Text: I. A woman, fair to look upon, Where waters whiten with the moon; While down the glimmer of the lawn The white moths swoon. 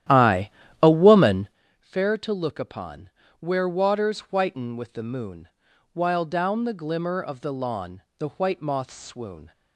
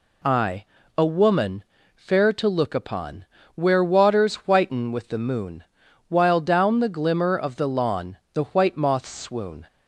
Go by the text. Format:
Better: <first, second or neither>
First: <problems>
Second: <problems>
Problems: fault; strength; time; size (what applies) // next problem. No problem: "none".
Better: second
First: starts louder than the rest; strong; until 1.6 s; 12 dB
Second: none